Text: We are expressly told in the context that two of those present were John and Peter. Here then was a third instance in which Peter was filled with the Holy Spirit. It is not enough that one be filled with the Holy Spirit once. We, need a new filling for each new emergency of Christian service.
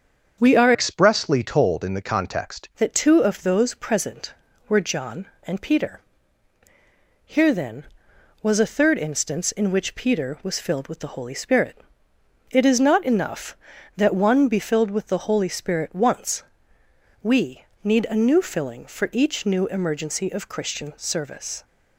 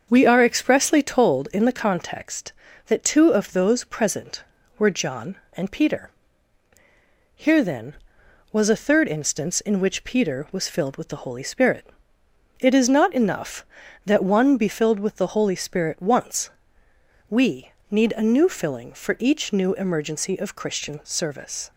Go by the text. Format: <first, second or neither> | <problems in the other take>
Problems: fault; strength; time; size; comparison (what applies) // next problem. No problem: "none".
second | starts louder than the rest; until 1.4 s; 7 dB; also in the second // changes voice from "expressly" to "context"; from 0.7 to 2.6 s; 1.9 s long